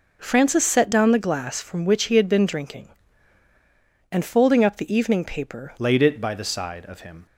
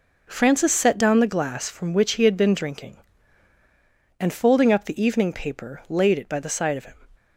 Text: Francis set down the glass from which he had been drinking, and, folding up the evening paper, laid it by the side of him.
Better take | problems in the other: second | changes voice at "laid"; from 5.7 s on; 1.5 s long

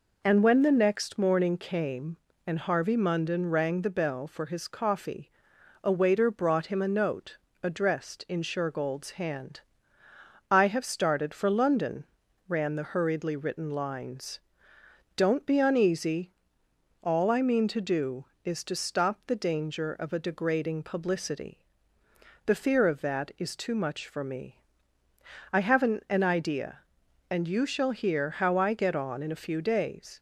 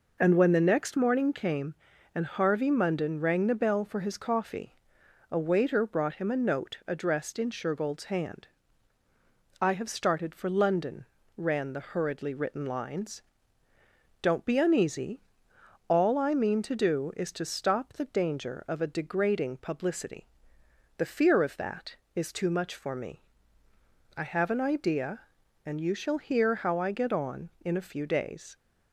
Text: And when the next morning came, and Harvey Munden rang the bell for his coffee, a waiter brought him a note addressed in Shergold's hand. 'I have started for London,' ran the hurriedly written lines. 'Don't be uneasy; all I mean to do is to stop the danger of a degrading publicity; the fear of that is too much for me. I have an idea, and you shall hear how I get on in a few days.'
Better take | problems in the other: second | pauses between "note" and "addressed"; slight; at 7.3 s; 0.26 s long // says "an" twice; at 26.0 s

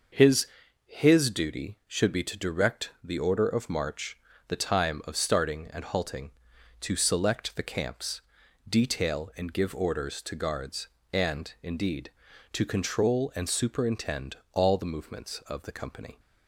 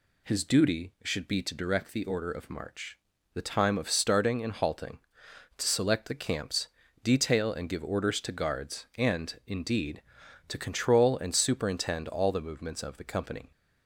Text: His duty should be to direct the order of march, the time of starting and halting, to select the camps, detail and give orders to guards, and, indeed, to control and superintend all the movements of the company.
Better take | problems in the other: second | says "His" twice; at 0.8 s // pauses between "superintend" and "all"; slight; at 14.3 s; 0.16 s long

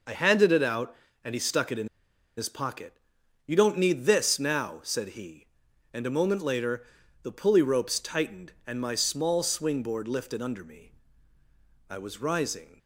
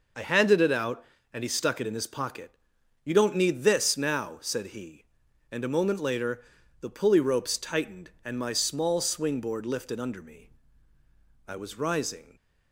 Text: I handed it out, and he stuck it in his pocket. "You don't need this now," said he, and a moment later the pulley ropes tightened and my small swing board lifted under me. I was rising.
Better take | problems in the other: second | pauses between "in" and "his"; noticeable; at 1.8 s; 0.50 s long // pauses between "later" and "the"; at 6.8 s; 0.38 s long; also in the second

